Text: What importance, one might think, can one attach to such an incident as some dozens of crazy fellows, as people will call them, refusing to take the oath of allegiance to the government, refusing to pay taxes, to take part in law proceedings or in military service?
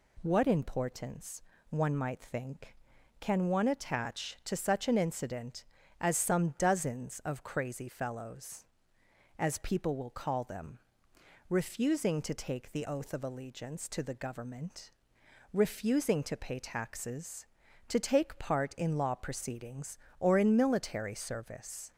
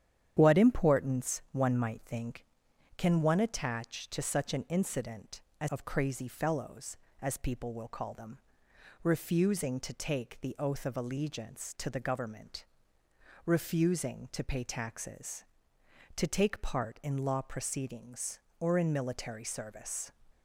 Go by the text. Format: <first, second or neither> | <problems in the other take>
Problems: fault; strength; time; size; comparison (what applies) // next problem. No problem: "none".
first | starts louder than the rest; strong; until 1.3 s; 9.5 dB // skips "some dozens"; at 5.6 s